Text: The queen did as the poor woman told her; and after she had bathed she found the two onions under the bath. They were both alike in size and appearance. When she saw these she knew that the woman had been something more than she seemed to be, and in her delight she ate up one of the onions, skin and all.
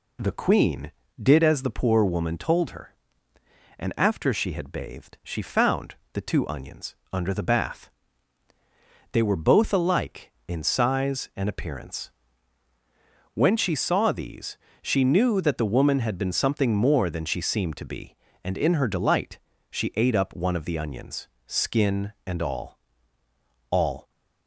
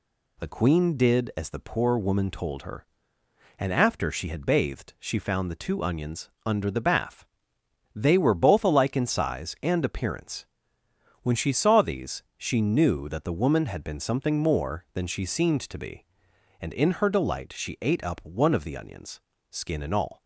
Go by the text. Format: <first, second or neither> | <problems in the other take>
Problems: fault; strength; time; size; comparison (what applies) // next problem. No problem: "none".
second | pauses between "found" and "the"; slight; at 5.9 s; 0.18 s long // pauses between "onions" and "under"; slight; at 6.9 s; 0.16 s long; slight in the second // pauses between "these" and "she"; slight; at 14.5 s; 0.24 s long // pauses between "delight" and "she"; slight; at 19.3 s; 0.32 s long // says "all" twice; at 23.6 s